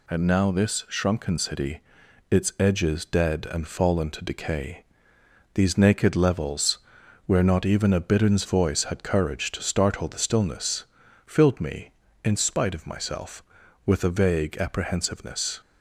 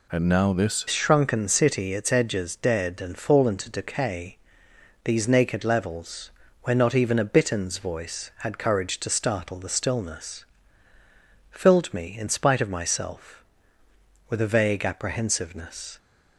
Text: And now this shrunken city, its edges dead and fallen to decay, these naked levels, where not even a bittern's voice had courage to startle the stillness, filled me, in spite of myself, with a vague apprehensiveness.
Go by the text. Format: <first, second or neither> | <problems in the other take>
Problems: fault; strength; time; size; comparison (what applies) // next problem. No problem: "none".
first | changes voice at "shrunken"; from 0.8 s on; 15.1 s long